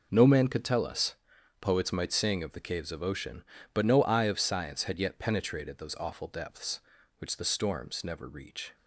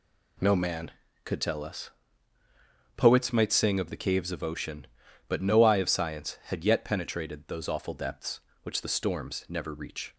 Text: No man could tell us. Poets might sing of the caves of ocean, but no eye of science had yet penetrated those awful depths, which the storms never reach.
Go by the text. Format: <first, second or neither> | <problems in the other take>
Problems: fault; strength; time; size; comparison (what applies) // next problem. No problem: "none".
neither | none